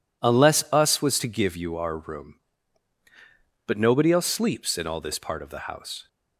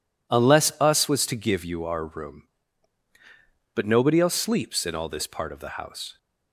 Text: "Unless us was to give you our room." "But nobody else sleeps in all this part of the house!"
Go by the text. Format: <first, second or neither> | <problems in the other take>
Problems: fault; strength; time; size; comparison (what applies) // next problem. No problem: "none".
neither | none